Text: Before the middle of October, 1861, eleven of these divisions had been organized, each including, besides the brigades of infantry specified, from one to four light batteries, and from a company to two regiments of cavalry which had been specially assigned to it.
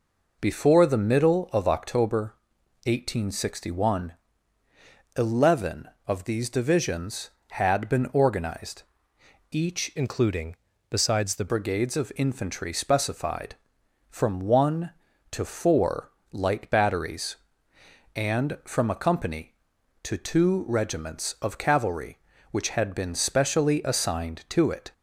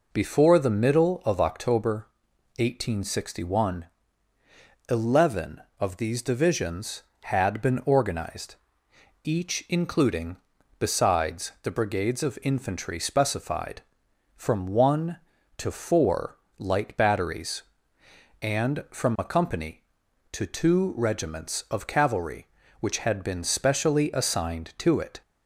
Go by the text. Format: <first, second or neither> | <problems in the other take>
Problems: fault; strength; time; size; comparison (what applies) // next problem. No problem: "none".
second | changes voice from "including" to "the"; from 9.9 to 11.4 s; 1.5 s long // pauses between "four" and "light"; slight; at 16.1 s; 0.22 s long; slight in the second